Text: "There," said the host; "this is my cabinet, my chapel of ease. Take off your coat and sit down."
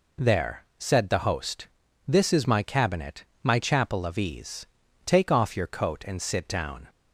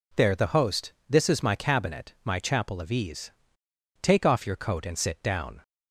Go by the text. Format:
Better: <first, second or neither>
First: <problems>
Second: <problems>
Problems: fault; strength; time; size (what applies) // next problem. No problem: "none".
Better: first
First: none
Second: skips "said"; at 0.3 s